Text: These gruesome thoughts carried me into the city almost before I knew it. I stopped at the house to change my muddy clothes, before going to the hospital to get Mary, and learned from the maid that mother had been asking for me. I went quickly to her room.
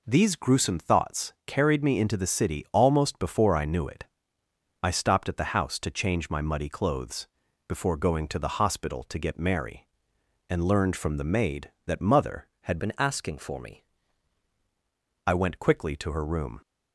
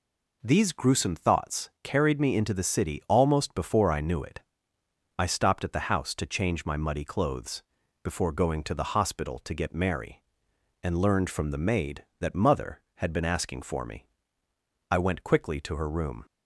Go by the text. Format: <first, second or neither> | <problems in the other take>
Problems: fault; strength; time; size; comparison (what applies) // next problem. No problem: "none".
second | changes voice from "been" to "me"; from 12.7 to 13.8 s; 1.1 s long